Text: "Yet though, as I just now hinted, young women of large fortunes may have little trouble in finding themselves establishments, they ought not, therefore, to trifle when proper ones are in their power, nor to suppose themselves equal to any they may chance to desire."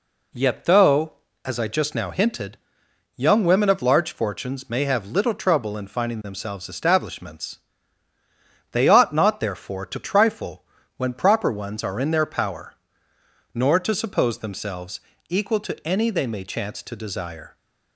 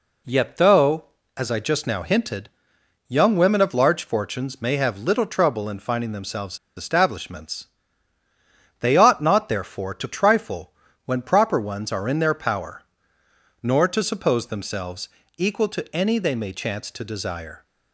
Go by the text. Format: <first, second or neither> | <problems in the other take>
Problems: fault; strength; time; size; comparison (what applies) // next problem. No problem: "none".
first | pauses between "themselves" and "establishments"; slight; at 6.5 s; 0.19 s long // pauses between "trifle" and "when"; slight; at 10.7 s; 0.34 s long; slight in the first // pauses between "themselves" and "equal"; slight; at 15.0 s; 0.30 s long; slight in the first